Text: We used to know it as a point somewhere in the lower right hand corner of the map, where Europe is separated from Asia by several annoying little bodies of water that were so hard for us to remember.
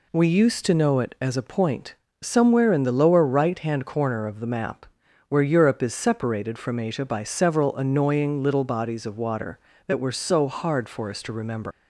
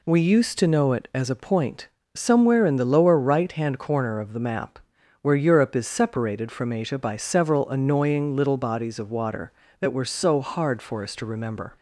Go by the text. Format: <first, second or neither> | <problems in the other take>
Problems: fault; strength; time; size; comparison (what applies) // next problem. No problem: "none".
second | pauses between "point" and "somewhere"; slight; at 1.9 s; 0.28 s long; slight in the second // leaves "remember" unfinished; at 11.7 s; 115 ms